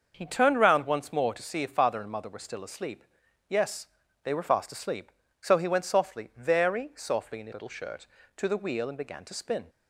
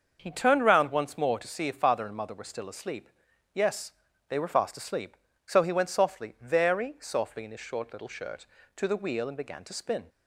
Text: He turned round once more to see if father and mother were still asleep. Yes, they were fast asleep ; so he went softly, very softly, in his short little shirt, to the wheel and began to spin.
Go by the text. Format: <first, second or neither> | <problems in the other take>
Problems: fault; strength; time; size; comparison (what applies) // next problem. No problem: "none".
second | starts louder than the rest; until 1.1 s; 6.5 dB; also in the second // skips "short"; at 7.5 s